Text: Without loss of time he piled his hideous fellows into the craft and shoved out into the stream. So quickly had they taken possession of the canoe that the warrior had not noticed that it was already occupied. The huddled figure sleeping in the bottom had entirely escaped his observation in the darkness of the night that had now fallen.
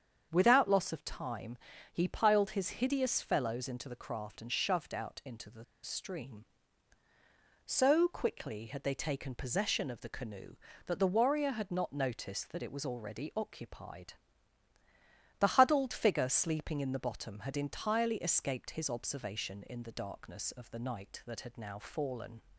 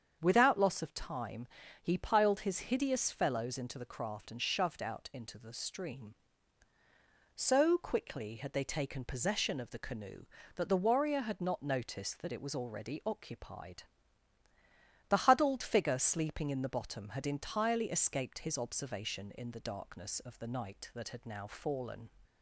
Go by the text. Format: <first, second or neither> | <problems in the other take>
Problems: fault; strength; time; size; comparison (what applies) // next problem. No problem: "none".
second | starts louder than the rest; strong; until 1.3 s; 7.5 dB; strong in the second // pauses between "time" and "he"; slight; at 1.5 s; 0.34 s long; slight in the second // pauses between "the" and "stream"; slight; at 5.6 s; 0.18 s long